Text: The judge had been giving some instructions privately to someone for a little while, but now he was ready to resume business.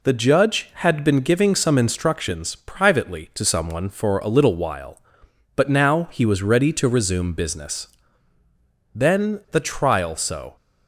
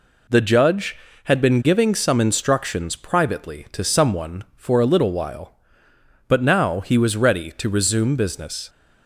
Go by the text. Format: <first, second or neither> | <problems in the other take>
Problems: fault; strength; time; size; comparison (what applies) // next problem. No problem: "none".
second | goes on to say "Then the trial so"; from 8.9 s on; 1.6 s long